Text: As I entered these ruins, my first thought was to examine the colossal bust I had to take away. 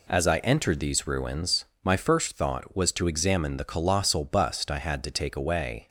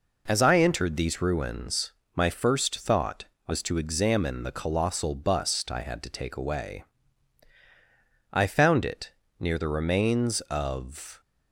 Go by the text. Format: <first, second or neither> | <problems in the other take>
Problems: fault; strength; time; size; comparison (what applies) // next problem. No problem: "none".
first | goes on to say "I found it near the remains of"; strong; from 8.3 s on; 2.8 s long